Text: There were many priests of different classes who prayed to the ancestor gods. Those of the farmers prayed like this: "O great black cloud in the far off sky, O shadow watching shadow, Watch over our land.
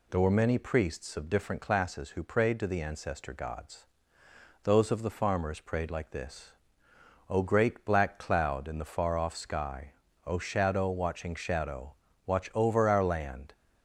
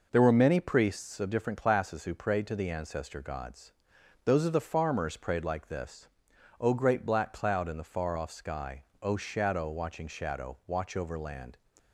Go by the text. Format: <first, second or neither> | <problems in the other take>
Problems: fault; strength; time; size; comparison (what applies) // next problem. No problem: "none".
first | skips "our"; at 11.1 s